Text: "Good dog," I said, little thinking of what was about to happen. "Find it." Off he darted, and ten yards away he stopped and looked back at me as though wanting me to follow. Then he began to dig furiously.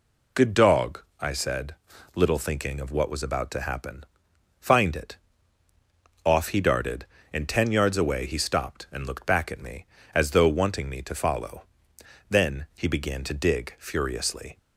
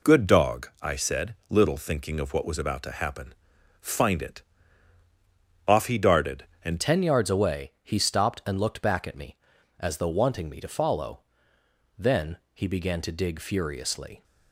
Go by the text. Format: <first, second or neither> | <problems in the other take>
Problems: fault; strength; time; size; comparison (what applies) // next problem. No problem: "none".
first | changes voice at "ten"; from 6.8 s on; 7.4 s long // pauses between "Then" and "he"; slight; at 12.3 s; 0.16 s long